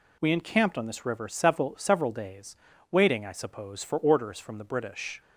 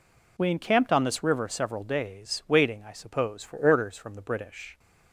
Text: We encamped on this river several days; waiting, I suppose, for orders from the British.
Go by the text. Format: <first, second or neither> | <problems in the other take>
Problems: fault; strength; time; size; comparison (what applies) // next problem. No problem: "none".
second | says "several" twice; at 1.7 s